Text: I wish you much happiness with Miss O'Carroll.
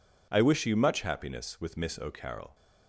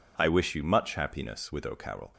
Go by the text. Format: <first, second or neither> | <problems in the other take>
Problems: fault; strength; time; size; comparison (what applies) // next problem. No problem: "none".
first | skips "Miss"; at 1.6 s